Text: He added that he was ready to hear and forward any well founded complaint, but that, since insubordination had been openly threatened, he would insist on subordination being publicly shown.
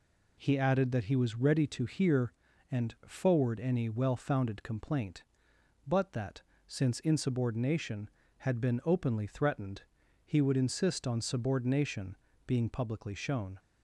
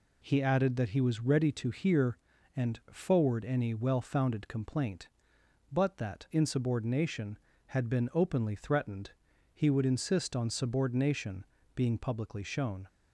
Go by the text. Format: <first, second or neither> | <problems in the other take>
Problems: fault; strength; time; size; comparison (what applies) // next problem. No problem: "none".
first | skips "since"; at 6.2 s // pauses between "subordination" and "being"; slight; at 11.4 s; 0.30 s long; slight in the first